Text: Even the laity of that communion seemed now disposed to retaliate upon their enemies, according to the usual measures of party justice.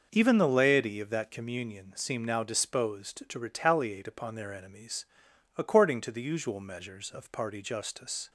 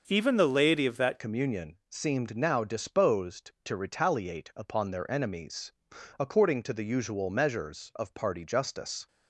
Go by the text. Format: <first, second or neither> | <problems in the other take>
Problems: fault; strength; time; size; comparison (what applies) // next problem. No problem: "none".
first | starts louder than the rest; noticeable; until 1.0 s; 6 dB // changes voice at "communion"; from 1.1 s on; 7.9 s long